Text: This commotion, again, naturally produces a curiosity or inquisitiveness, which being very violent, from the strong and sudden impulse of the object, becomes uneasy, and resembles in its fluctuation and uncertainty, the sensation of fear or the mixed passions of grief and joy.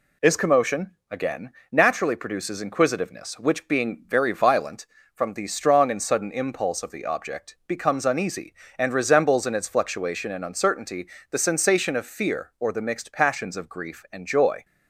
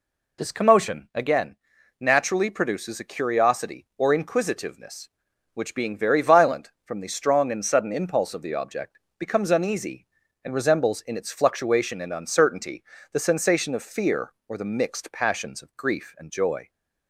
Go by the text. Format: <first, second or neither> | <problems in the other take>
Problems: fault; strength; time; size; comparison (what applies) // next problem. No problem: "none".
second | skips "a curiosity or"; at 2.6 s